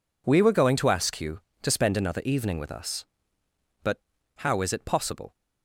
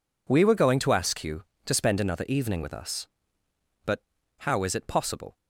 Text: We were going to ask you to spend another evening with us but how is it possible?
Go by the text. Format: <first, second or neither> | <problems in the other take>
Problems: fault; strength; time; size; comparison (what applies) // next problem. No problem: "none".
neither | pauses between "but" and "how"; the same in both